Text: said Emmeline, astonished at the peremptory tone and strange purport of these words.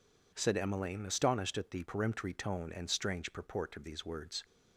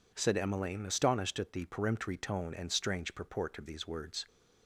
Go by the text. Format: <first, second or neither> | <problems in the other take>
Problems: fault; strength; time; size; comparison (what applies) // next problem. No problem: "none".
neither | none